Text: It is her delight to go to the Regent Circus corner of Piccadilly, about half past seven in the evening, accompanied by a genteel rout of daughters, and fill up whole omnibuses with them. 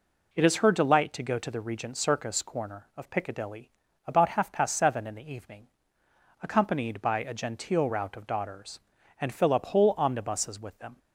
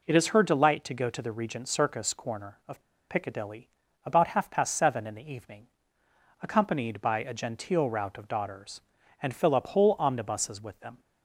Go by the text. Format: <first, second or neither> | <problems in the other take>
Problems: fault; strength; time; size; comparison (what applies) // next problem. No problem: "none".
first | pauses between "of" and "Piccadilly"; slight; at 2.8 s; 0.28 s long